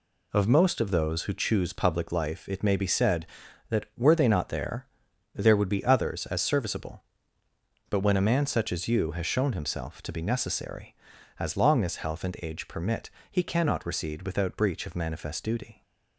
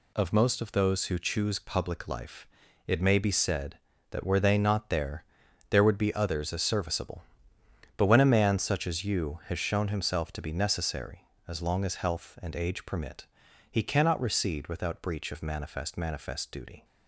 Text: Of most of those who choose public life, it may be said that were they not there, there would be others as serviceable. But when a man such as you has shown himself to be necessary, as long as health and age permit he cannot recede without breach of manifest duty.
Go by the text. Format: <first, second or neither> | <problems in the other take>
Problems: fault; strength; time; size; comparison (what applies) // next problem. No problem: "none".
first | pauses between "permit" and "he"; noticeable; at 13.2 s; 0.46 s long; slight in the first // says "manifest" twice; at 15.9 s